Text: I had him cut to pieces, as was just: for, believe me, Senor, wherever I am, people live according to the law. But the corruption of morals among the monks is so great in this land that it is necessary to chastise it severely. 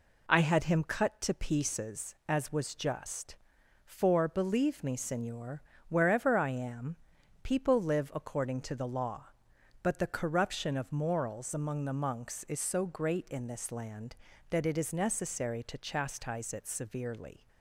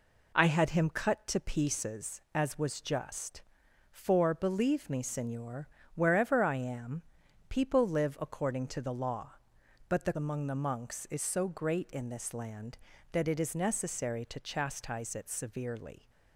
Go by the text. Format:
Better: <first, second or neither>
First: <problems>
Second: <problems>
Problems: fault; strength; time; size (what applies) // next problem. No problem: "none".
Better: first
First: none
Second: skips "corruption of morals"; at 10.1 s